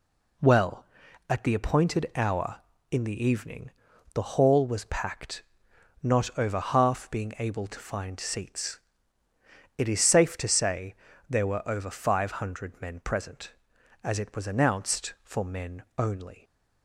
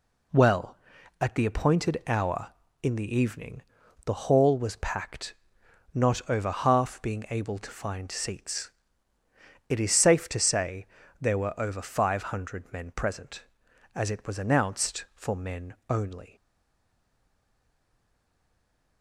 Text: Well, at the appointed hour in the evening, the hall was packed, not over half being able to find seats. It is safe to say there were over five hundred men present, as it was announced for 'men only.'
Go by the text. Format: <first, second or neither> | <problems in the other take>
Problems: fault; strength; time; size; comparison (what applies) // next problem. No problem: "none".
first | pauses between "say" and "there"; slight; at 10.8 s; 0.34 s long; slight in the first // pauses between "men" and "only"; slight; at 15.7 s; 0.16 s long; slight in the first // stays silent after the last word; strong; from 16.3 s on; 2.7 s long